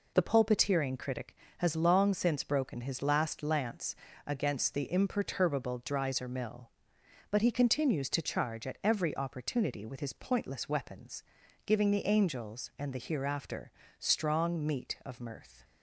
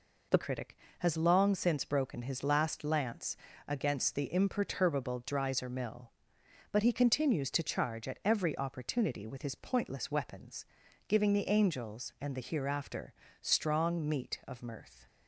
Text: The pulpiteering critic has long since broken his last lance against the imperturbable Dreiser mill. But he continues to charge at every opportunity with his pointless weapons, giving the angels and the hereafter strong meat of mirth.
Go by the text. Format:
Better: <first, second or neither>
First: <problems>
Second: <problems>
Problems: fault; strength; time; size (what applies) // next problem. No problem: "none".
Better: first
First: pauses between "lance" and "against"; slight; at 3.9 s; 0.32 s long // pauses between "hereafter" and "strong"; slight; at 13.7 s; 0.28 s long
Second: skips "pulpiteering"; at 0.3 s // pauses between "lance" and "against"; slight; at 3.3 s; 0.32 s long // pauses between "hereafter" and "strong"; slight; at 13.1 s; 0.28 s long